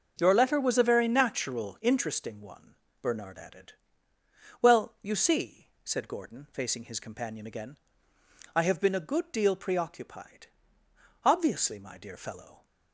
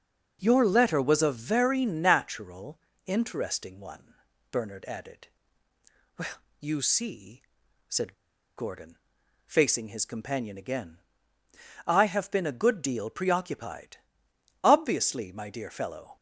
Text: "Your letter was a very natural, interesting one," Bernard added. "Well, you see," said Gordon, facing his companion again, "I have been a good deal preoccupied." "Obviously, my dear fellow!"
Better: first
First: starts louder than the rest; noticeable; until 1.1 s; 6 dB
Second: starts louder than the rest; noticeable; until 1.4 s; 6 dB // pauses between "said" and "Gordon"; at 8.1 s; 0.43 s long

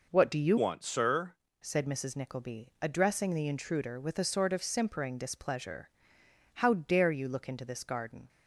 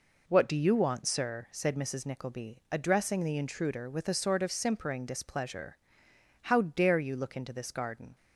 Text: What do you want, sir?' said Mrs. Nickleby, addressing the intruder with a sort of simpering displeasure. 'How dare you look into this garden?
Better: second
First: changes voice from "want" to "sir"; from 0.5 to 1.3 s; 0.8 s long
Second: none

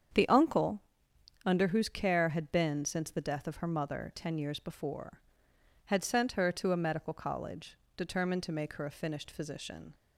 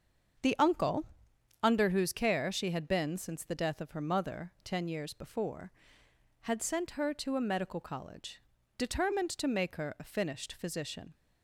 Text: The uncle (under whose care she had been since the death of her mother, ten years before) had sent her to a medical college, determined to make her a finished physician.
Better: second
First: starts louder than the rest; strong; until 1.7 s; 8 dB // skips "she"; at 2.2 s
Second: starts louder than the rest; until 2.0 s; 6.5 dB

